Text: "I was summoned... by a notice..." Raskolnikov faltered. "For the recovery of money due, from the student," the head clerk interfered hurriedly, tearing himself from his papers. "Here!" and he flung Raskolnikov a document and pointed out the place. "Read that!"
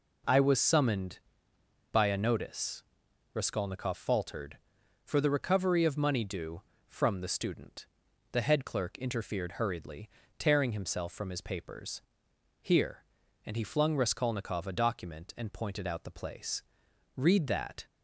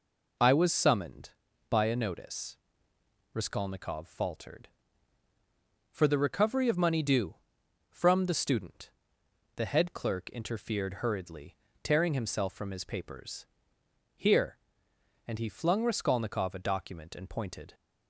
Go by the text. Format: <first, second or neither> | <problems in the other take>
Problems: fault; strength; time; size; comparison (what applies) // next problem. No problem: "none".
first | stops before "out the place Read that"; at 17.7 s